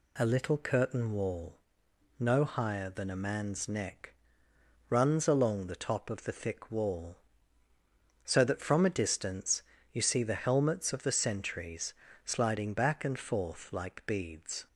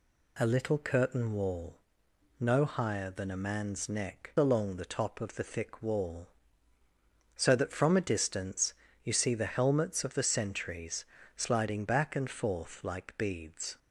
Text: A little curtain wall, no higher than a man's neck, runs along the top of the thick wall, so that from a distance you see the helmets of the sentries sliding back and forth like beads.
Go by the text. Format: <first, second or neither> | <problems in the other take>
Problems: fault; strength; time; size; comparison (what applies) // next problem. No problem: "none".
first | skips "runs"; at 4.3 s // pauses between "distance" and "you"; slight; at 8.7 s; 0.30 s long; slight in the first // pauses between "sentries" and "sliding"; slight; at 11.0 s; 0.30 s long; slight in the first